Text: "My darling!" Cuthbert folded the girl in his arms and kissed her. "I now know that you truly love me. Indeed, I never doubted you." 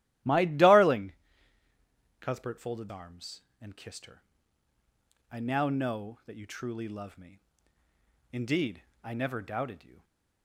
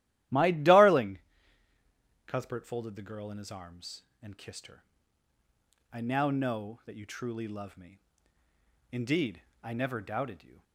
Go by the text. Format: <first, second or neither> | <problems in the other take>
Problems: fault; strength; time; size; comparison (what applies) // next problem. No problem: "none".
second | starts louder than the rest; strong; until 2.3 s; 14.5 dB; strong in the second // skips "the girl in his"; at 2.8 s // stays silent after the last word; slight; from 9.9 s on; 0.5 s long